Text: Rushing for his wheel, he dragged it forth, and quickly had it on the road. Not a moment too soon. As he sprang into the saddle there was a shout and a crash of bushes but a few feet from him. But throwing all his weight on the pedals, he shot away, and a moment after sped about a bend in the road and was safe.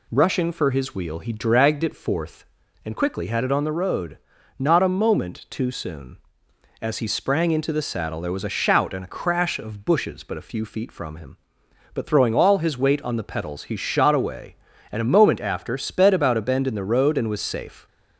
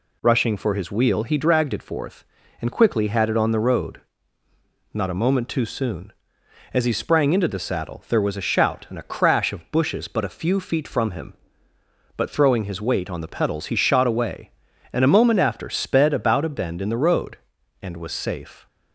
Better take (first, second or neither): first